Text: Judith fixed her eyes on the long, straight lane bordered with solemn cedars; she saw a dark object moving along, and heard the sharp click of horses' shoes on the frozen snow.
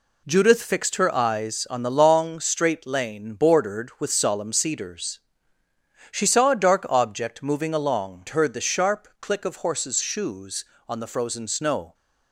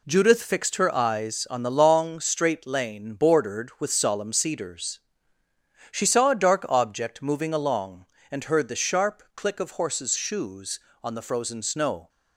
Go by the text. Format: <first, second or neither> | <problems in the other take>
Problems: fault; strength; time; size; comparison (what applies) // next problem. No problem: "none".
second | skips "and"; at 8.2 s